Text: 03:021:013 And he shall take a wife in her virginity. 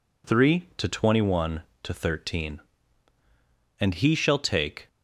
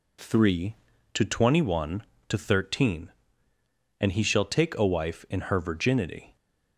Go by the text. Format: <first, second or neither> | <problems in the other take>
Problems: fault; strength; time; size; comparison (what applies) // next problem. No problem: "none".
second | stops before "a wife in her virginity"; at 4.8 s